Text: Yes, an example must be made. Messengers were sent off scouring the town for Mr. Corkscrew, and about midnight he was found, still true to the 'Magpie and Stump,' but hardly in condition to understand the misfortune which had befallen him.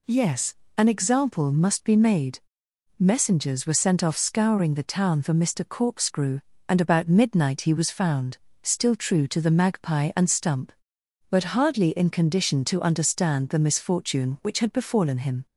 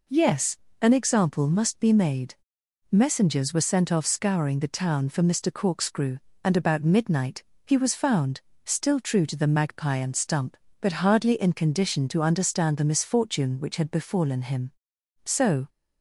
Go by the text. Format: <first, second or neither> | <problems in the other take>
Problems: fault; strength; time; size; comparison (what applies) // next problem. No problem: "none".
first | pauses between "midnight" and "he"; slight; at 7.4 s; 0.22 s long // goes on to say "So"; slight; from 15.2 s on; 0.44 s long